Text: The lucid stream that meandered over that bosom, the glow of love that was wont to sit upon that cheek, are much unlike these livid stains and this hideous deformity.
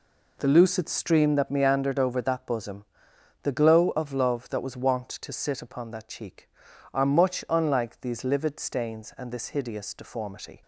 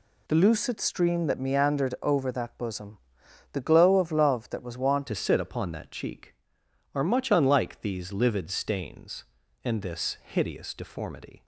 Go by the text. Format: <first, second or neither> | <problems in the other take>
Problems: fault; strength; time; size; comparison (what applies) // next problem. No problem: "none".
first | changes voice at "to"; from 5.0 s on; 6.4 s long